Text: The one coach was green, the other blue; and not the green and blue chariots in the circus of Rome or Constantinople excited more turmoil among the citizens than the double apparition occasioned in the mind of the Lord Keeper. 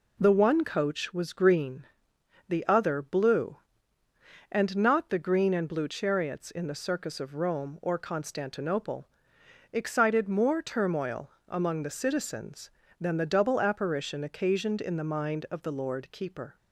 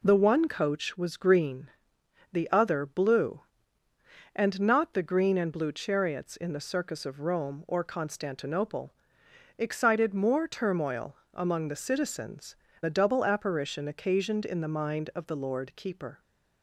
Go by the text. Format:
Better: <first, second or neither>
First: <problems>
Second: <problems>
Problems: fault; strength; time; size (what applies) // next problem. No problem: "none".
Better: first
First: pauses between "Constantinople" and "excited"; noticeable; at 9.0 s; 0.66 s long // pauses between "turmoil" and "among"; slight; at 11.2 s; 0.18 s long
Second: pauses between "Constantinople" and "excited"; noticeable; at 8.9 s; 0.66 s long // pauses between "turmoil" and "among"; slight; at 11.1 s; 0.18 s long // skips "than"; at 12.6 s